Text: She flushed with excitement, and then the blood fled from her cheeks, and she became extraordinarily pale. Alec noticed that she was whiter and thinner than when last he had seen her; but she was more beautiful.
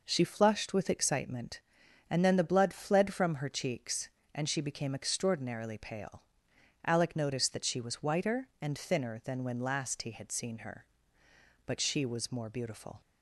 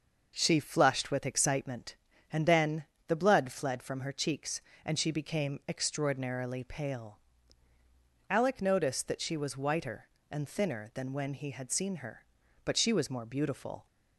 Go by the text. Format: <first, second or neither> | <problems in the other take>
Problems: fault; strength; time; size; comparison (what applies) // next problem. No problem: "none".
first | starts louder than the rest; noticeable; until 1.3 s; 6 dB // pauses between "then" and "the"; slight; at 2.8 s; 0.20 s long // skips "last"; at 11.3 s